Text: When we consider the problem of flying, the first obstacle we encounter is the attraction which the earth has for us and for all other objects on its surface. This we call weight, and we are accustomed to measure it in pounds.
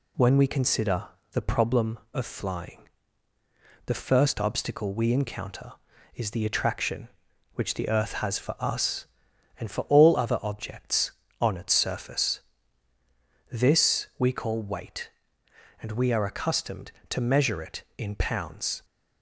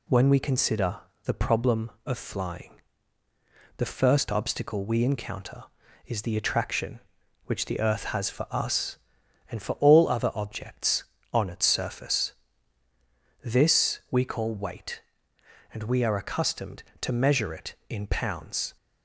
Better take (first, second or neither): neither